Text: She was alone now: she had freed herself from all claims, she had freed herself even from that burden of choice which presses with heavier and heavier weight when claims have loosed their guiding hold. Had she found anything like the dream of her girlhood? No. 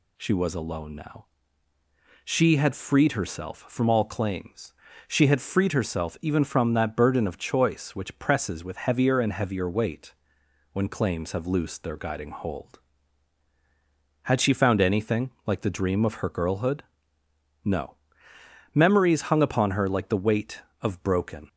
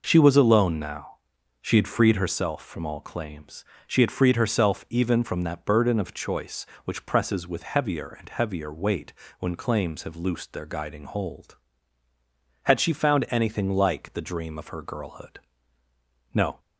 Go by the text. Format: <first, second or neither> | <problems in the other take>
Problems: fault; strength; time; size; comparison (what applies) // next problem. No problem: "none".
second | pauses between "weight" and "when"; noticeable; at 10.1 s; 0.58 s long; slight in the second // goes on to say "Memories hung upon her like the weight of broken"; strong; from 18.7 s on; 2.7 s long